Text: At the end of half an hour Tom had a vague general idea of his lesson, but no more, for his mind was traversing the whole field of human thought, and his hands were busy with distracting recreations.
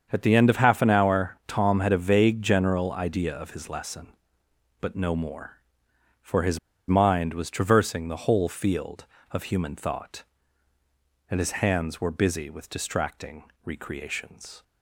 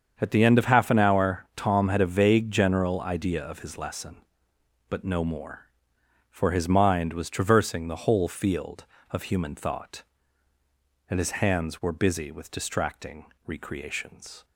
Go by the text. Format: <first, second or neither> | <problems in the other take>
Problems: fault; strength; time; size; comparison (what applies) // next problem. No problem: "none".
second | starts louder than the rest; until 1.1 s; 7 dB; also in the second // pauses between "his" and "mind"; slight; at 6.5 s; 0.30 s long // pauses between "distracting" and "recreations"; slight; at 13.4 s; 0.20 s long; slight in the second